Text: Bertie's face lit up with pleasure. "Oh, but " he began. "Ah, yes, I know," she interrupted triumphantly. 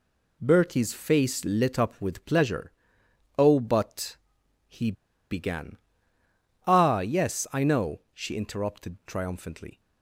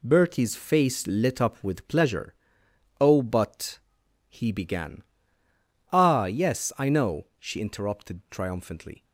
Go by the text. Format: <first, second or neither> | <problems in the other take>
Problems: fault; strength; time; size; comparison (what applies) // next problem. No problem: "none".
second | pauses between "he" and "began"; at 4.8 s; 0.42 s long